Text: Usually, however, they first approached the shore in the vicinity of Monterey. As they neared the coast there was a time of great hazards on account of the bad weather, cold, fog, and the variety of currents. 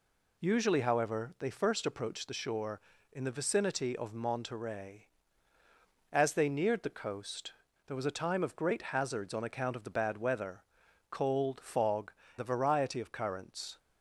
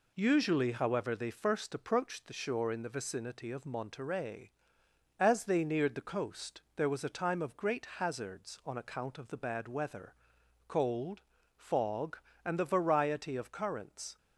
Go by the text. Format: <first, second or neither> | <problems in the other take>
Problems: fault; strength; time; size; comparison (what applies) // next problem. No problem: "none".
second | pauses between "coast" and "there"; slight; at 7.5 s; 0.34 s long // skips "and"; at 12.2 s